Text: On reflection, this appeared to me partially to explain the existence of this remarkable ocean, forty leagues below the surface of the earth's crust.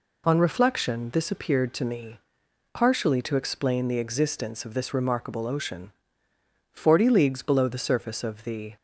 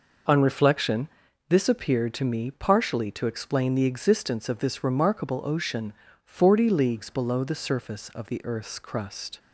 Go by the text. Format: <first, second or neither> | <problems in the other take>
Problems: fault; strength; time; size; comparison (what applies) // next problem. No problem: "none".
second | pauses between "me" and "partially"; noticeable; at 2.1 s; 0.54 s long // stops before "earth's crust"; at 8.7 s